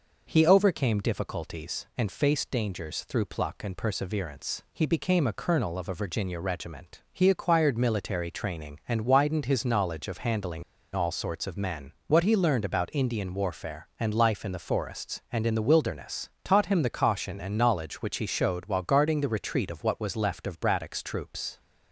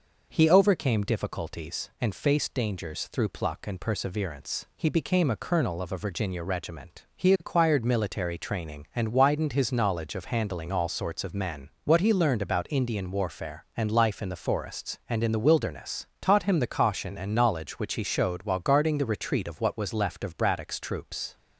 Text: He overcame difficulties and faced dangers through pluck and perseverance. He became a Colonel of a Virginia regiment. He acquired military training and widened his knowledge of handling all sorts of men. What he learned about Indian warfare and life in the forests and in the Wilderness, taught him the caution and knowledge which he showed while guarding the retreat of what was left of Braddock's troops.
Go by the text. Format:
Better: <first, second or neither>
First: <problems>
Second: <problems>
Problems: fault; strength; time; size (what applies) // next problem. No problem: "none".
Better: second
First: pauses between "handling" and "all"; slight; at 10.6 s; 0.32 s long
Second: none